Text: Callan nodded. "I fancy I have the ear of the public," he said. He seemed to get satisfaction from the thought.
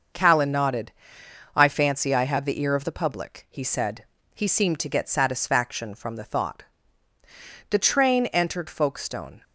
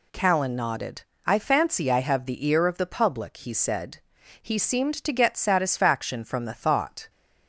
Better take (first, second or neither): second